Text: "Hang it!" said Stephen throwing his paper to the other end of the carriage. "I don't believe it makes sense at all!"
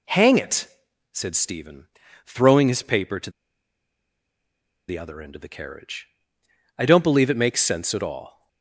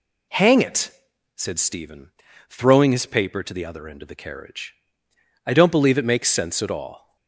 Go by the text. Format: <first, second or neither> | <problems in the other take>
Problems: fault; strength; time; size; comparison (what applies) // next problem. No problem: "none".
second | pauses between "Stephen" and "throwing"; at 1.8 s; 0.40 s long; also in the second // pauses between "to" and "the"; strong; at 3.2 s; 1.5 s long